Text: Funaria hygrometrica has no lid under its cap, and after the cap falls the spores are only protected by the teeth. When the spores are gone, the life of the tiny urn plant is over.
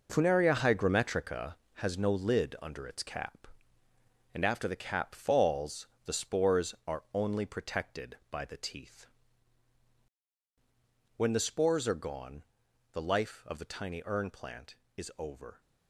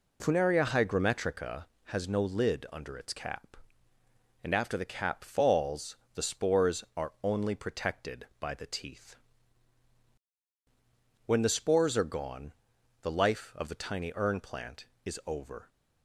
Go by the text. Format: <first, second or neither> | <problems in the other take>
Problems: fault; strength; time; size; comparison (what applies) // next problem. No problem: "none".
second | gets quieter; strong; throughout; 10 dB // pauses between "falls" and "the"; slight; at 5.8 s; 0.18 s long; slight in the second